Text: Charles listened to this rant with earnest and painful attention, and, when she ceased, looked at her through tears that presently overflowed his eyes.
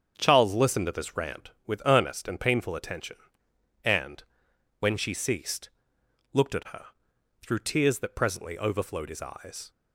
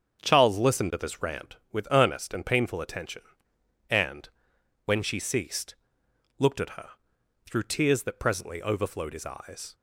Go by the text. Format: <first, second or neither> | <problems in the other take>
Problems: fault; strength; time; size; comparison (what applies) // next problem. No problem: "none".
neither | starts louder than the rest; strong; the same in both // pauses between "her" and "through"; noticeable; the same in both